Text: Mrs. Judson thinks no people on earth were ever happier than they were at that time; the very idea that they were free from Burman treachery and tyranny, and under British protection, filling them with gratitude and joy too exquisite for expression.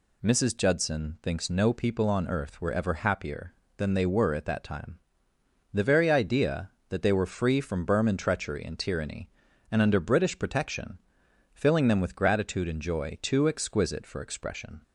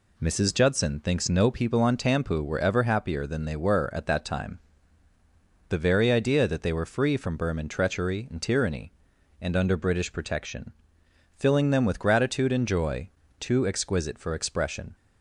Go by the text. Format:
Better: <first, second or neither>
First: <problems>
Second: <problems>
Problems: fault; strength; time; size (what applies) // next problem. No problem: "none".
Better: first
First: none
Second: says "tampu" for "earth"; at 1.9 s // pauses between "joy" and "too"; slight; at 13.1 s; 0.28 s long